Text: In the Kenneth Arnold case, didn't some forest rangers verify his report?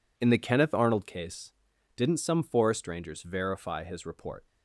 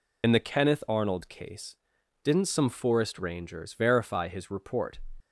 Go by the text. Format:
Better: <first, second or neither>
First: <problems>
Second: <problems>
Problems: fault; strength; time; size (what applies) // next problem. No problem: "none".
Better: first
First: none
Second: loses the start of "In"; at 0.2 s; 55 ms